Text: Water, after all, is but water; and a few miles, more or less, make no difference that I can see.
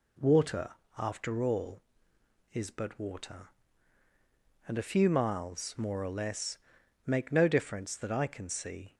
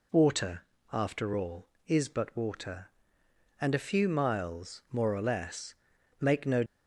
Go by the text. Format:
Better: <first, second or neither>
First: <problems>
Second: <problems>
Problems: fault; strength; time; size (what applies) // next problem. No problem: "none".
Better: first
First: none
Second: stops before "difference that I can see"; at 6.6 s